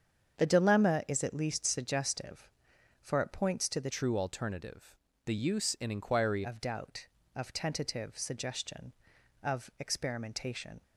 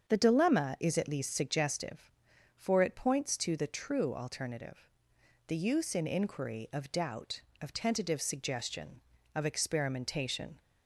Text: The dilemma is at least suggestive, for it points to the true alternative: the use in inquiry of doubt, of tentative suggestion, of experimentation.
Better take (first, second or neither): second